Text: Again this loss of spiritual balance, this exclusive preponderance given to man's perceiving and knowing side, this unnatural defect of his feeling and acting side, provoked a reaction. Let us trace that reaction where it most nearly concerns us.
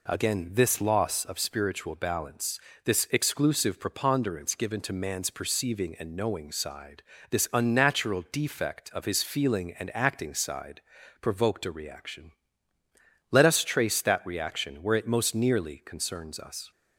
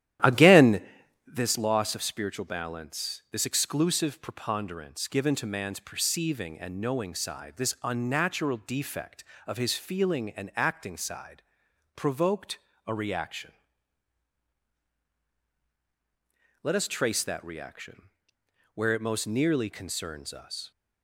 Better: first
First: none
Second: starts louder than the rest; strong; until 1.4 s; 12 dB // pauses between "Again" and "this"; noticeable; at 0.8 s; 0.52 s long // pauses between "provoked" and "a"; slight; at 12.5 s; 0.26 s long // pauses between "reaction" and "where"; noticeable; at 18.0 s; 0.66 s long

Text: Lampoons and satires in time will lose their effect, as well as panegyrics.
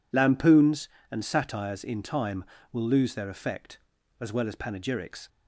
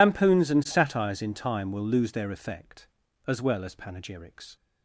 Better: first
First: none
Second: loses the start of "Lampoons"; at 0.0 s; 140 ms

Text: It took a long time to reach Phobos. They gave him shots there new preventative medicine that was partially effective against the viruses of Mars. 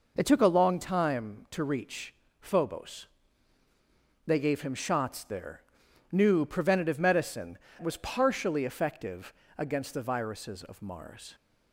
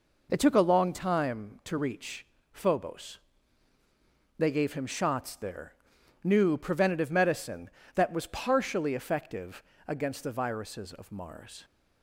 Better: second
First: pauses between "reach" and "Phobos"; slight; at 2.1 s; 0.26 s long // pauses between "there" and "new"; noticeable; at 5.6 s; 0.50 s long // skips "that"; at 7.6 s // pauses between "effective" and "against"; slight; at 9.3 s; 0.24 s long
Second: pauses between "reach" and "Phobos"; slight; at 2.2 s; 0.26 s long // pauses between "there" and "new"; noticeable; at 5.7 s; 0.50 s long // pauses between "effective" and "against"; slight; at 9.6 s; 0.24 s long

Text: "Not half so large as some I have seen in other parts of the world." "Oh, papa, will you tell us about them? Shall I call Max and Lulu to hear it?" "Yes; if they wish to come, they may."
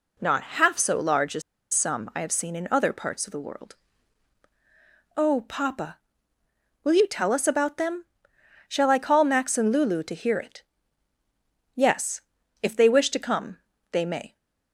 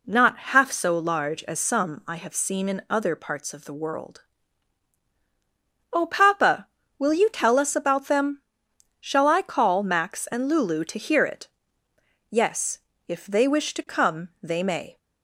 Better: second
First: pauses between "as" and "some"; slight; at 1.4 s; 0.32 s long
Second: none

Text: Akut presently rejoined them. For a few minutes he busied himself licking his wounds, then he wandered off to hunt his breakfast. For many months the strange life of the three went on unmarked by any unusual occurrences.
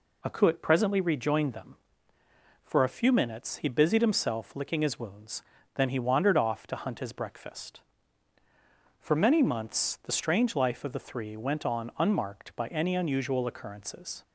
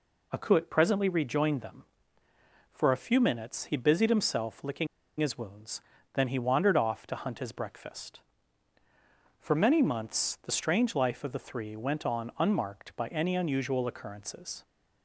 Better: first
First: none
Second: pauses between "licking" and "his"; slight; at 4.8 s; 0.33 s long

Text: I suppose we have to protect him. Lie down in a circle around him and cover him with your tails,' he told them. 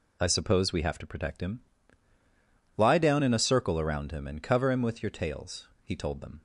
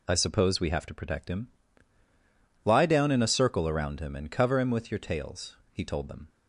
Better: neither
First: none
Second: none

